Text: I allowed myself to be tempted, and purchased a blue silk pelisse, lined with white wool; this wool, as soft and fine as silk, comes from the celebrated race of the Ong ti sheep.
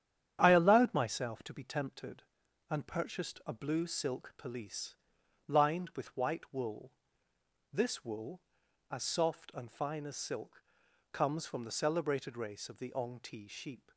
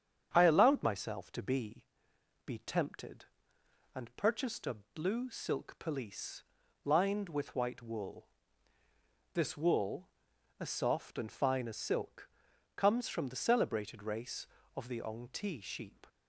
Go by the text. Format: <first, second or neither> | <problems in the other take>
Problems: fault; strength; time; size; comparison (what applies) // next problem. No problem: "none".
first | starts louder than the rest; strong; until 1.3 s; 8 dB; strong in the first // says "be" twice; at 2.4 s // pauses between "a" and "blue"; slight; at 4.7 s; 0.20 s long